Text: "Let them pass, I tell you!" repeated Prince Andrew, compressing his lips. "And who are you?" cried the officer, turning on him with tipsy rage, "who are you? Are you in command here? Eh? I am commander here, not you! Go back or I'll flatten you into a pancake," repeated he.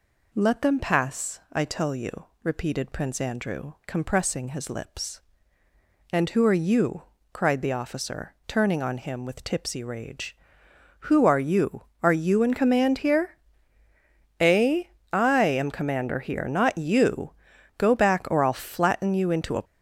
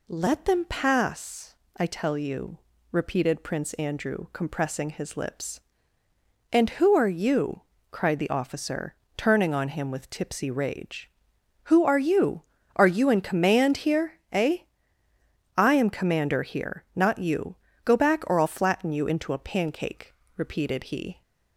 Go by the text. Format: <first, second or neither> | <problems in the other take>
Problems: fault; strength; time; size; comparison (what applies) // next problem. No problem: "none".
second | stops before "pancake repeated he"; at 19.6 s